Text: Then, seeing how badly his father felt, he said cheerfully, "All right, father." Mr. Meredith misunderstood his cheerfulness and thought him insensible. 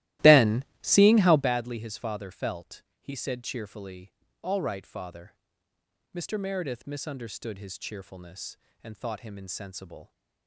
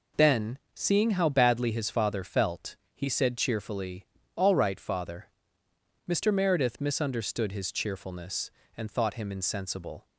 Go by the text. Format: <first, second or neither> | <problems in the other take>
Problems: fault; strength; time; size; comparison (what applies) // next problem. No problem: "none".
second | starts louder than the rest; strong; until 1.5 s; 16 dB